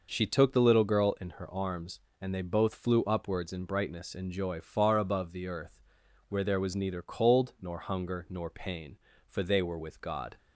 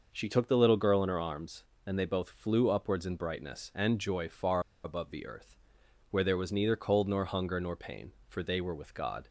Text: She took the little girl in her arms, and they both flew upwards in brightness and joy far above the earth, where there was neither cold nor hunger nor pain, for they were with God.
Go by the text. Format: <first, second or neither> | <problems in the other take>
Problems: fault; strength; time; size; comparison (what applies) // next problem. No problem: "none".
first | pauses between "far" and "above"; slight; at 4.5 s; 0.24 s long